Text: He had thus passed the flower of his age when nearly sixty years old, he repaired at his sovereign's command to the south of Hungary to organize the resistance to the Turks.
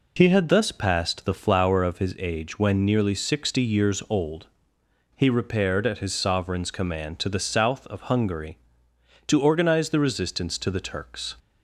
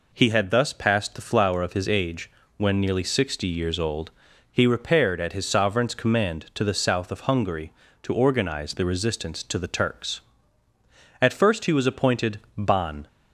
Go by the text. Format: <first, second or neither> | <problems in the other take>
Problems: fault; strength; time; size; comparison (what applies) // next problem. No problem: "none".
first | pauses between "age" and "when"; slight; at 2.2 s; 0.28 s long // goes on to say "At first he was appointed Ban"; strong; from 11.1 s on; 1.8 s long